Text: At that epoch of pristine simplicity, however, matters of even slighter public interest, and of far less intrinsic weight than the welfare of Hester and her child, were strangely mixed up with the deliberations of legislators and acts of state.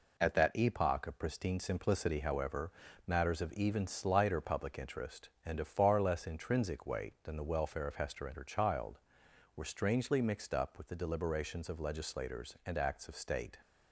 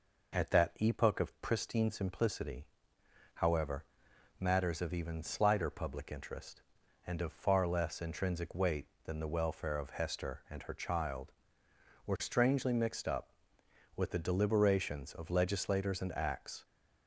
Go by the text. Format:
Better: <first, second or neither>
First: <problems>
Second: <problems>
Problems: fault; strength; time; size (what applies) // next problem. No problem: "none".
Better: first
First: none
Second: stops before "of state"; at 16.6 s